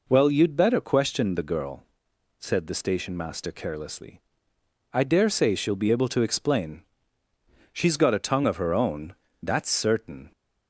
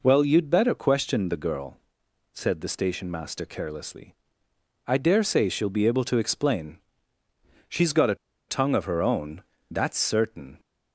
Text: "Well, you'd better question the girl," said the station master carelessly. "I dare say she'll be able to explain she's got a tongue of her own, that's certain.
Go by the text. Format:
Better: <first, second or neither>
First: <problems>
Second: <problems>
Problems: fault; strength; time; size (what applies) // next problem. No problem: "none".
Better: first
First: pauses between "explain" and "she's"; noticeable; at 6.8 s; 0.90 s long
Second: pauses between "explain" and "she's"; noticeable; at 6.7 s; 0.90 s long // pauses between "a" and "tongue"; slight; at 8.1 s; 0.34 s long